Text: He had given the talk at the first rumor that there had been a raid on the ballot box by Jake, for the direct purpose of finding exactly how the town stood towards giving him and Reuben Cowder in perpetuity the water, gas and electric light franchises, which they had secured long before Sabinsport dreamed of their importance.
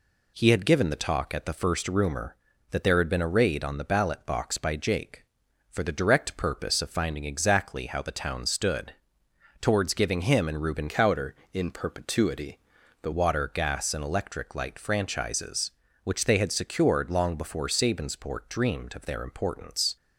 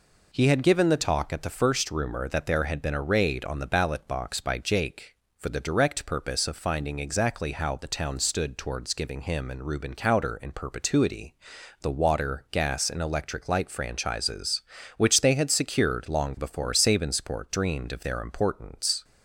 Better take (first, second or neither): second